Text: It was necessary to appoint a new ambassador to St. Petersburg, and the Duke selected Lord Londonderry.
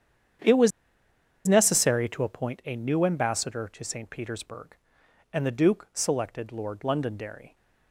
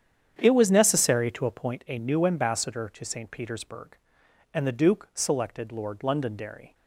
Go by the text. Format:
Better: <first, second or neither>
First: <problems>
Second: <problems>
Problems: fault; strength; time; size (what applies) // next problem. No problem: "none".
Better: second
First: starts louder than the rest; strong; until 2.1 s; 9 dB // pauses between "was" and "necessary"; noticeable; at 0.7 s; 0.76 s long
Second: starts louder than the rest; strong; until 1.3 s; 9 dB